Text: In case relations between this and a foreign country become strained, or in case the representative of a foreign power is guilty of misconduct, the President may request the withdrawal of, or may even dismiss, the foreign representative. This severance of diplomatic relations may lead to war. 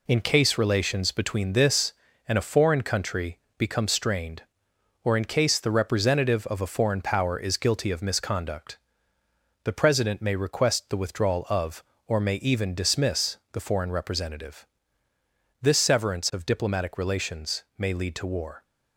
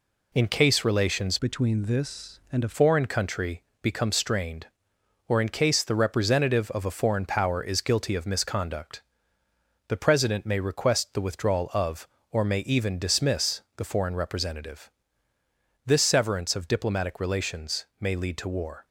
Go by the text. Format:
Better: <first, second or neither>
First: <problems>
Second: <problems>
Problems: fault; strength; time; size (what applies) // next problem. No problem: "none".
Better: first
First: pauses between "country" and "become"; slight; at 3.3 s; 0.18 s long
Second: changes voice from "between" to "a"; from 1.3 to 2.7 s; 1.4 s long // pauses between "country" and "become"; slight; at 3.6 s; 0.18 s long